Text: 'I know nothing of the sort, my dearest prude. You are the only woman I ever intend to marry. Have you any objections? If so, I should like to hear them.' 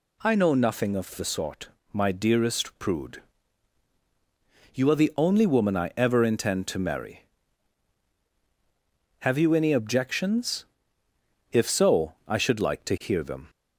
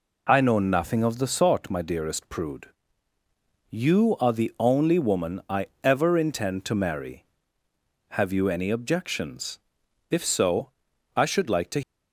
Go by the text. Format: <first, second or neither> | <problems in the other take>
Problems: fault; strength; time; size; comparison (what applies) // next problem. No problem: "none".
first | pauses between "I" and "ever"; slight; at 5.6 s; 0.18 s long // stops before "hear them"; at 11.8 s